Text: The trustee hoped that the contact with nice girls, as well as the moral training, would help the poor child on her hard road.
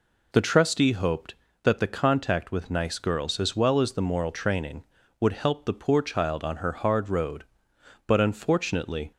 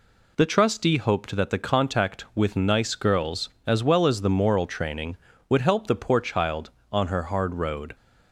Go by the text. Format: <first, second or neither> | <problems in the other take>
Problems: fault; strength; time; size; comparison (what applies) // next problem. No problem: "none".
second | goes on to say "But unfortunately"; noticeable; from 8.0 s on; 1.0 s long